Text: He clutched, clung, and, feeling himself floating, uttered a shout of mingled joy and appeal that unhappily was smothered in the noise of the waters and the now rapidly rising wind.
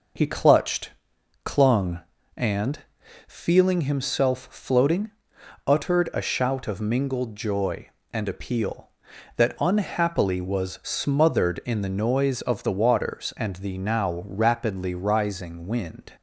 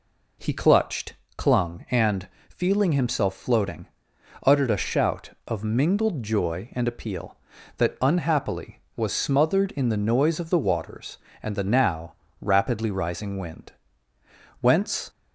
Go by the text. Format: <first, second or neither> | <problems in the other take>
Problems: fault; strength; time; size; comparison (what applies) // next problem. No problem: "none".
first | pauses between "now" and "rapidly"; slight; at 12.1 s; 0.26 s long // goes on to say "Whence"; slight; from 14.6 s on; 0.48 s long